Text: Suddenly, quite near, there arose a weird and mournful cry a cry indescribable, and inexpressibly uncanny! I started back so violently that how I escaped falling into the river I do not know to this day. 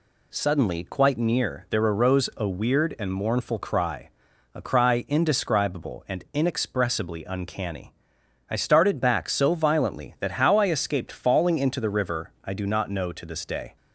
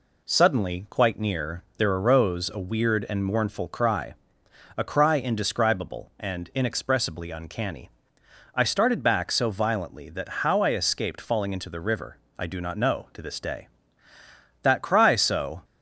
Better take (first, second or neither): first